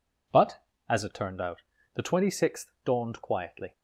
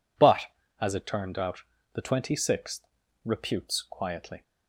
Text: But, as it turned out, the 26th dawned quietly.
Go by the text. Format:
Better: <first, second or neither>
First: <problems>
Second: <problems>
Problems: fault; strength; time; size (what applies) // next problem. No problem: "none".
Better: first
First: none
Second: says "reputes" for "dawned"; at 3.2 s